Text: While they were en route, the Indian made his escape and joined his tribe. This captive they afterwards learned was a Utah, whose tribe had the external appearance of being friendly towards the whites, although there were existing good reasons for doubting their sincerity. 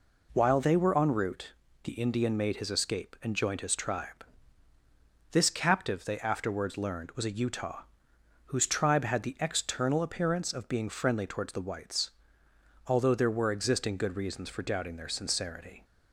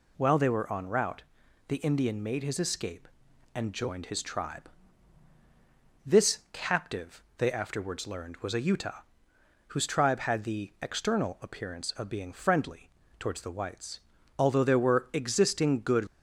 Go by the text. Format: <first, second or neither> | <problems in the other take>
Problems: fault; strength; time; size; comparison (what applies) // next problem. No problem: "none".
first | pauses between "captive" and "they"; slight; at 7.2 s; 0.16 s long // pauses between "friendly" and "towards"; slight; at 12.8 s; 0.30 s long // stops before "reasons for doubting their sincerity"; at 16.0 s